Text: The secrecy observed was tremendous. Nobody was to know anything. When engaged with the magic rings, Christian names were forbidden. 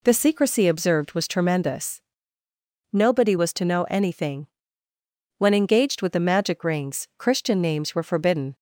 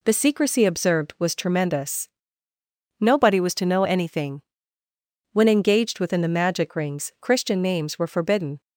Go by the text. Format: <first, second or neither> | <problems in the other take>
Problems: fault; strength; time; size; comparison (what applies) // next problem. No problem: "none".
first | says "within" for "with"; at 6.0 s